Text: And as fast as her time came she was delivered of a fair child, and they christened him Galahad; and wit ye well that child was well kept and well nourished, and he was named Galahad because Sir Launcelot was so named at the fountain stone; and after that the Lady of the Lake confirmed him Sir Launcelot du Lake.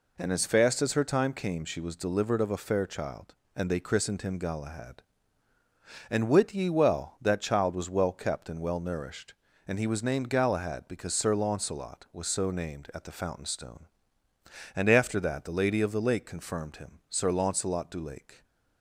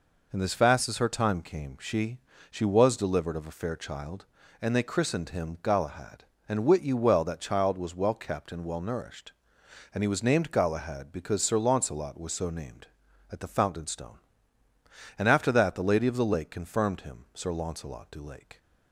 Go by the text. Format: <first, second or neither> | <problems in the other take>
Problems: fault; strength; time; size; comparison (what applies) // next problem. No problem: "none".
first | says "she" twice; at 2.5 s